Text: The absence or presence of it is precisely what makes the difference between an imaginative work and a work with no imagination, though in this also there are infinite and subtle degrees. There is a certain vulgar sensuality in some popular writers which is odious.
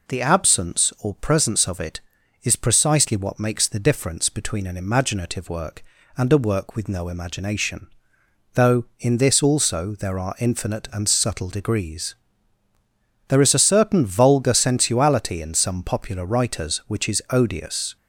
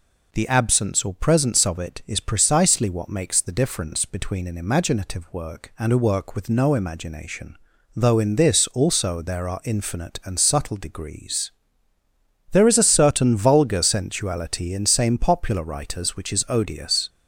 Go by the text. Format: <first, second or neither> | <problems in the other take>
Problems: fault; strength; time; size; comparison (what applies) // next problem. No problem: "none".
first | says "same" for "some"; at 14.8 s